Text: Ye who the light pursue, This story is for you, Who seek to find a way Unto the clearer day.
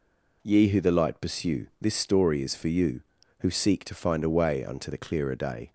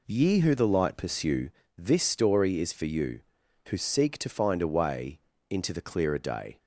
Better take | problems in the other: first | says "Into" for "Unto"; at 5.4 s

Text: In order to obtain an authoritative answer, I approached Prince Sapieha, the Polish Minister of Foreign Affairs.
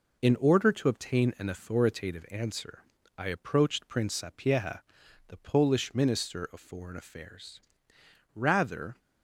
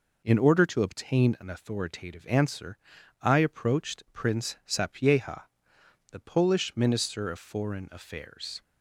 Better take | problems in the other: second | goes on to say "Rather"; noticeable; from 8.3 s on; 0.64 s long

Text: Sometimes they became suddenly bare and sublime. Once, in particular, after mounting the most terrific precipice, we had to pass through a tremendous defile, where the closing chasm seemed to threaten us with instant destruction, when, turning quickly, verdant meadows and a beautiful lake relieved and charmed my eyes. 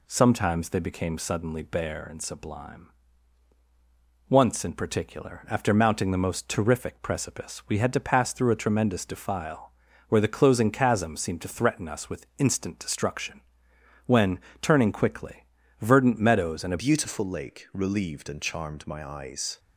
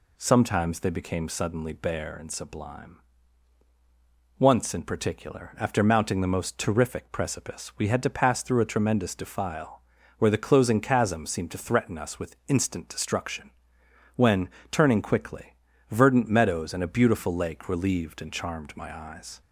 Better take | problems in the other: second | changes voice at "beautiful"; from 16.7 s on; 2.8 s long

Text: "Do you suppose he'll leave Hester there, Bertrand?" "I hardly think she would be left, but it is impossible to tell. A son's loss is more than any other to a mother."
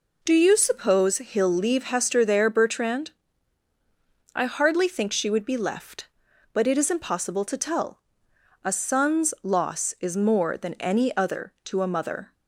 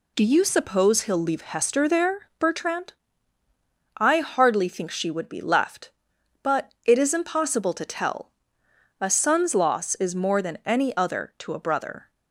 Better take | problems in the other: first | says "brother" for "mother"; at 11.5 s

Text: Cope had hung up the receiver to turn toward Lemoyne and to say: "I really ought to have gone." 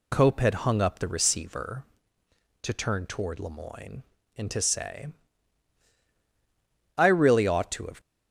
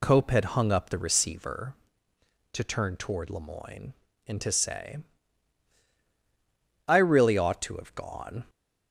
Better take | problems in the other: second | stops before "gone"; at 8.0 s

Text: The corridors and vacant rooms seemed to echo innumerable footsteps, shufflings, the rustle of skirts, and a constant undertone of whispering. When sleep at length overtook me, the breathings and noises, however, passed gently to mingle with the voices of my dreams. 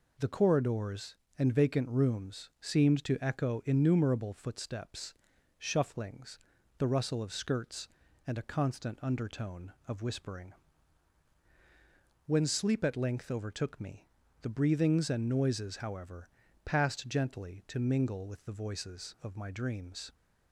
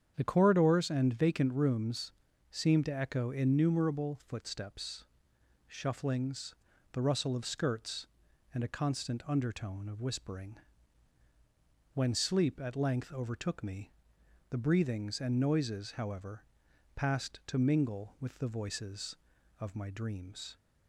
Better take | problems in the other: first | starts louder than the rest; strong; until 1.1 s; 8 dB // pauses between "rooms" and "seemed"; slight; at 2.1 s; 0.36 s long // skips "gently"; at 17.4 s

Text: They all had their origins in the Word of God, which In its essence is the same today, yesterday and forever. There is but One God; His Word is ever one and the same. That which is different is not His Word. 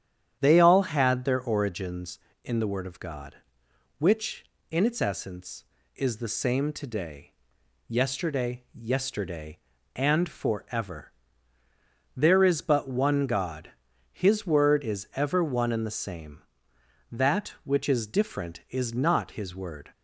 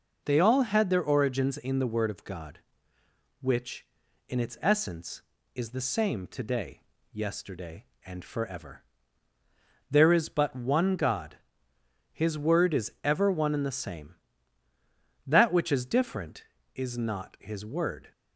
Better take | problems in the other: second | starts louder than the rest; strong; until 1.4 s; 9.5 dB // says "yesterday" twice; at 8.7 s

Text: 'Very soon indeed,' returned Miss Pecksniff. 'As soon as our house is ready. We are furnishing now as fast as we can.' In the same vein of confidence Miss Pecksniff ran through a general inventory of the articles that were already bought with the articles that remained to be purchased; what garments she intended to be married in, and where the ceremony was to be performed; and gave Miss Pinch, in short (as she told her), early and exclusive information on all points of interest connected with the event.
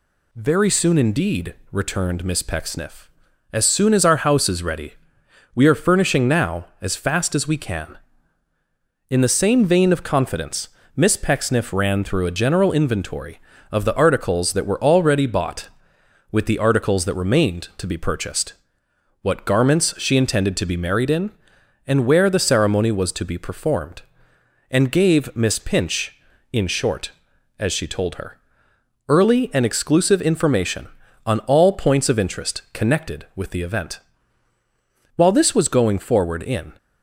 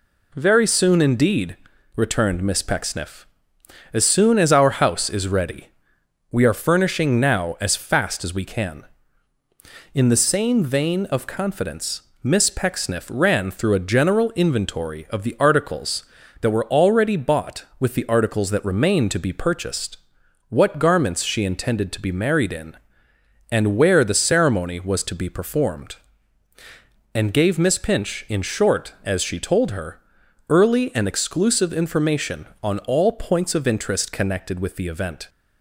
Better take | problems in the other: second | pauses between "confidence" and "Miss"; slight; at 10.6 s; 0.26 s long; slight in the second // goes on to say "While this was going forward in"; from 35.1 s on; 1.5 s long

